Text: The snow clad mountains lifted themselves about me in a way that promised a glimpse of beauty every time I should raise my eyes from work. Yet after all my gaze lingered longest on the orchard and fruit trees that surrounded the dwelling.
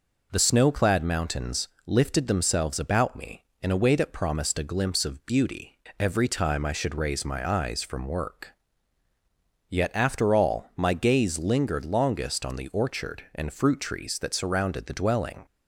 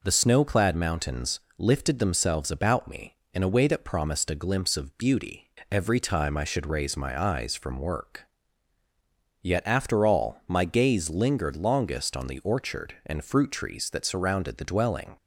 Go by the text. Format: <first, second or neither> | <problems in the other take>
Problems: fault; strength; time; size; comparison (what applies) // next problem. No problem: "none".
neither | pauses between "mountains" and "lifted"; slight; the same in both // pauses between "beauty" and "every"; slight; the same in both